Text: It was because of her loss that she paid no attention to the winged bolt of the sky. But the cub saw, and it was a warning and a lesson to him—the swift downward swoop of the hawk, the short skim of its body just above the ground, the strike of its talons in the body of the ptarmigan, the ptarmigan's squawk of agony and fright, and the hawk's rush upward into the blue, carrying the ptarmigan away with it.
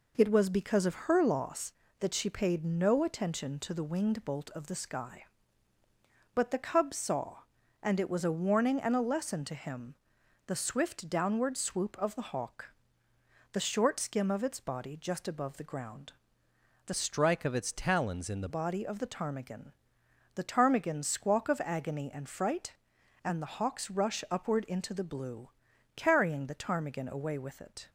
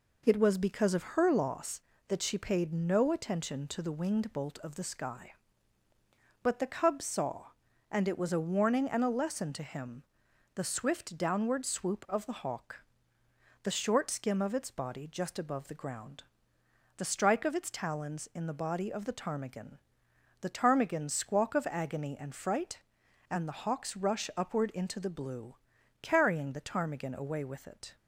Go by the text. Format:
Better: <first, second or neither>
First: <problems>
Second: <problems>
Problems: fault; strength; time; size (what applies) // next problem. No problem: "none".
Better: second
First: changes voice from "strike" to "the"; from 16.9 to 18.4 s; 1.5 s long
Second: none